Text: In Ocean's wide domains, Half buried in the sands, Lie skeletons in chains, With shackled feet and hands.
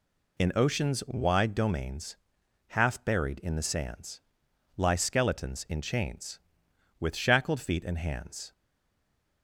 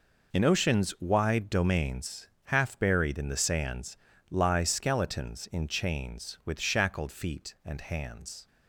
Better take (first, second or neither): second